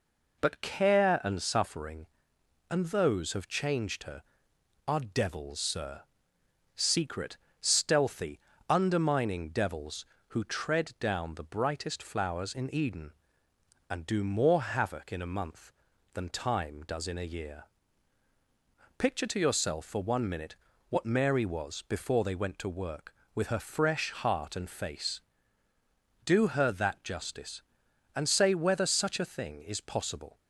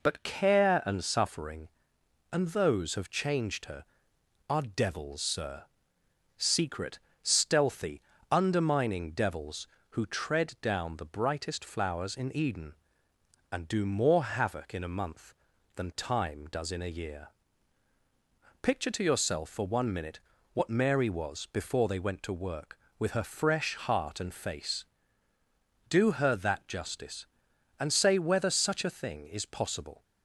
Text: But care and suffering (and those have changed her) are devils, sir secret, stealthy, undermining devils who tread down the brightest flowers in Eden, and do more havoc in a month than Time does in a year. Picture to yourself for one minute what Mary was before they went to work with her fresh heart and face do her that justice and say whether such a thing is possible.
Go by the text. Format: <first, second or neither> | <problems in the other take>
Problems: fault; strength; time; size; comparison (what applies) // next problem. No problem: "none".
neither | pauses between "sir" and "secret"; noticeable; the same in both // pauses between "minute" and "what"; slight; the same in both